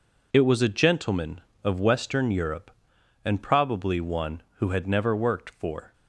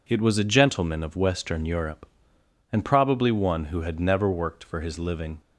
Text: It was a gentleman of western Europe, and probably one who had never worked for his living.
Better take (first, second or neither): second